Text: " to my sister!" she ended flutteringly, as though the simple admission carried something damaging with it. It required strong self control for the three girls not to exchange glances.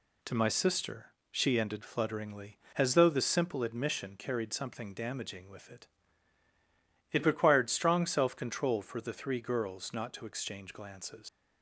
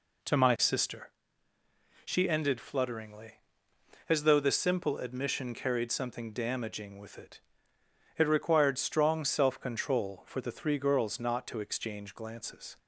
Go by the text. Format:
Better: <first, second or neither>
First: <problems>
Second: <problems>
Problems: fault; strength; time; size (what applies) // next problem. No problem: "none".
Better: second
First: leaves "glances" unfinished; at 11.2 s; 95 ms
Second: none